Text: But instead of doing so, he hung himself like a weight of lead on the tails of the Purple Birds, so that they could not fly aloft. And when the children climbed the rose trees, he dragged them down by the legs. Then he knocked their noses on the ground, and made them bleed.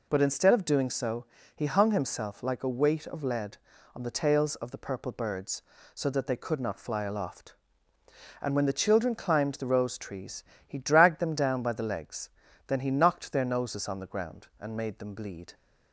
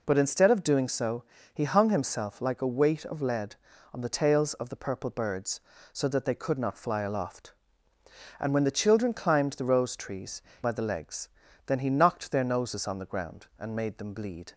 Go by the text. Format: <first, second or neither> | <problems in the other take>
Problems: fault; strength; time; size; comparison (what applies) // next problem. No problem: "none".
first | skips "he dragged them down"; at 10.5 s